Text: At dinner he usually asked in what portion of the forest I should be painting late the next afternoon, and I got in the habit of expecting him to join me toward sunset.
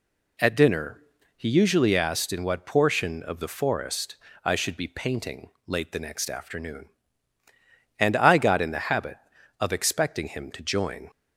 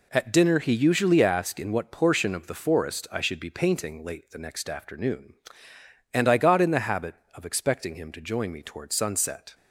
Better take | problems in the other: second | pauses between "dinner" and "he"; slight; at 1.0 s; 0.36 s long // pauses between "forest" and "I"; slight; at 4.1 s; 0.28 s long // pauses between "painting" and "late"; slight; at 5.5 s; 0.16 s long // stops before "me toward sunset"; at 11.1 s

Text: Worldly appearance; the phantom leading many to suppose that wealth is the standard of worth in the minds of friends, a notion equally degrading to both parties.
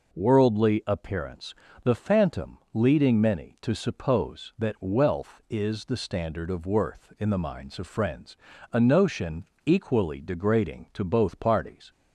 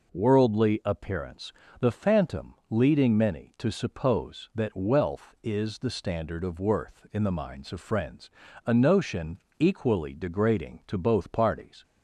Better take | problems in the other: neither | pauses between "phantom" and "leading"; slight; the same in both // pauses between "notion" and "equally"; slight; the same in both

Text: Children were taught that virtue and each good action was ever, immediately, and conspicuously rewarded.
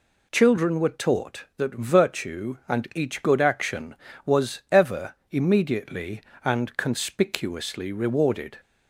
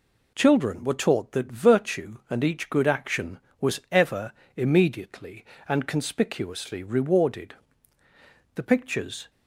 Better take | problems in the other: first | goes on to say "The pictures"; noticeable; from 8.5 s on; 0.74 s long

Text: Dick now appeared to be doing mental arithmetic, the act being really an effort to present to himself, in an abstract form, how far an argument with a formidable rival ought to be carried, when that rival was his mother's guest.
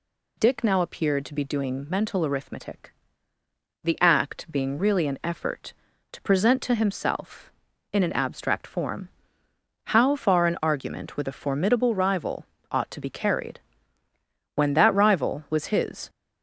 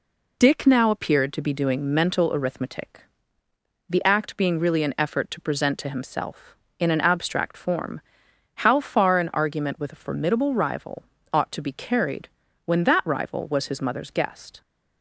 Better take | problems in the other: second | pauses between "rival" and "ought"; slight; at 12.4 s; 0.26 s long; slight in the second // stops before "mother's guest"; at 16.0 s

